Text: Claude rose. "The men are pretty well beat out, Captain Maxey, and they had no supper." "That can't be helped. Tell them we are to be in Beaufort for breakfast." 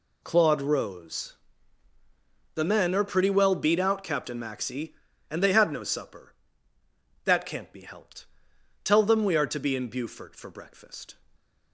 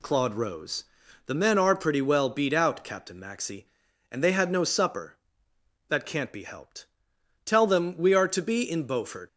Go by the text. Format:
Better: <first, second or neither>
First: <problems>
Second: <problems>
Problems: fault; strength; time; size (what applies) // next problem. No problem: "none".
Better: first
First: none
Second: stops before "for breakfast"; at 9.2 s